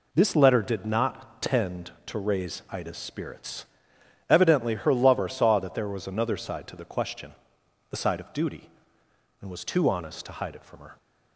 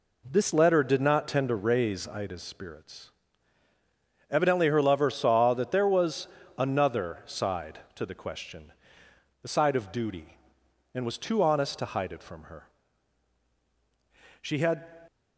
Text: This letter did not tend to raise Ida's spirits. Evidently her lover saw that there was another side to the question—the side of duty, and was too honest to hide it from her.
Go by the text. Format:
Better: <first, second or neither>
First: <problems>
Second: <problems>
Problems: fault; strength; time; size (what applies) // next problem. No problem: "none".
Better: first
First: none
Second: pauses between "was" and "another"; slight; at 6.2 s; 0.30 s long // goes on to say "She had"; from 14.4 s on; 0.54 s long